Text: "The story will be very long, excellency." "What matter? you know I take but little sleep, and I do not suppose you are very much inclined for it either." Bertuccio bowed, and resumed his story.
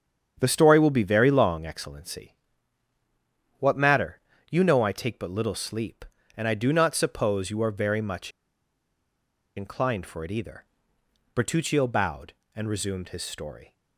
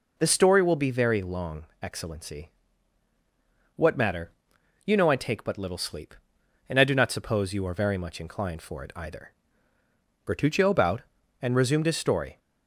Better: second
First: starts louder than the rest; strong; until 1.4 s; 8 dB // pauses between "much" and "inclined"; strong; at 8.3 s; 1.2 s long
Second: none

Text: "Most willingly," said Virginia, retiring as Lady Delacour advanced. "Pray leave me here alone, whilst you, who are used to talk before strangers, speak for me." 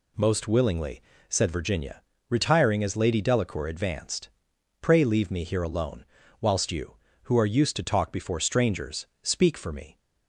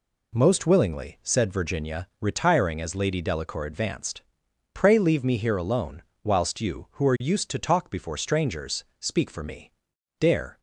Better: first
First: none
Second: goes on to say "Dare"; slight; from 10.1 s on; 0.40 s long

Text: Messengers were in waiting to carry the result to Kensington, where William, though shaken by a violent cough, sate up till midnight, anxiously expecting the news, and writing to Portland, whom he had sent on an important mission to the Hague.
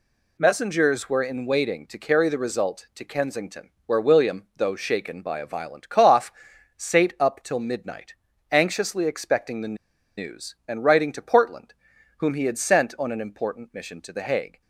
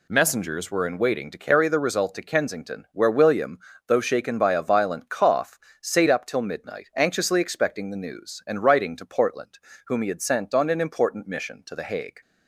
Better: second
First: pauses between "the" and "news"; at 9.7 s; 0.43 s long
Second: none

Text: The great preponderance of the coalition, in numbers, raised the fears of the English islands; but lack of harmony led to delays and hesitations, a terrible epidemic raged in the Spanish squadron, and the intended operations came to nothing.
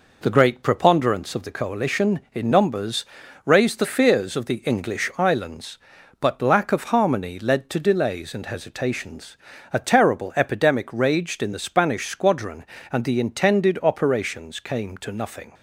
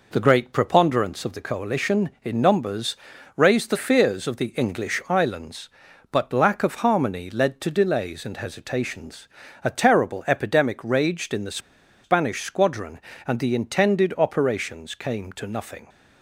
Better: first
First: none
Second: pauses between "the" and "Spanish"; at 11.5 s; 0.45 s long

